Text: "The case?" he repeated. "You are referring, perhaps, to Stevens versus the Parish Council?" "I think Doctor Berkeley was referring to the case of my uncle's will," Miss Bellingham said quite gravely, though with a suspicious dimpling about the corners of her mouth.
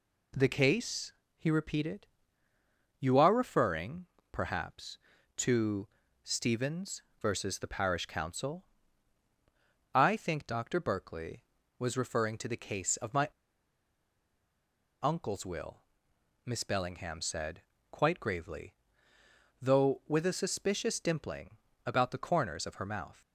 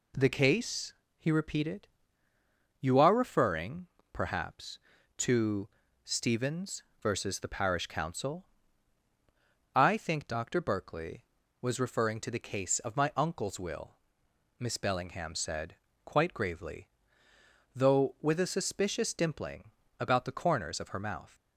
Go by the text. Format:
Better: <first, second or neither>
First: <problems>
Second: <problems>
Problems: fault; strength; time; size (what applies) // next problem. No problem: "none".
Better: second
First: pauses between "to" and "Stevens"; at 5.8 s; 0.38 s long // pauses between "Stevens" and "versus"; slight; at 7.0 s; 0.18 s long // pauses between "my" and "uncle's"; strong; at 13.2 s; 1.7 s long // pauses between "said" and "quite"; slight; at 17.6 s; 0.30 s long // pauses between "dimpling" and "about"; slight; at 21.5 s; 0.28 s long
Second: pauses between "to" and "Stevens"; at 5.6 s; 0.38 s long // pauses between "Stevens" and "versus"; slight; at 6.8 s; 0.18 s long // pauses between "said" and "quite"; slight; at 15.7 s; 0.30 s long // pauses between "dimpling" and "about"; slight; at 19.7 s; 0.28 s long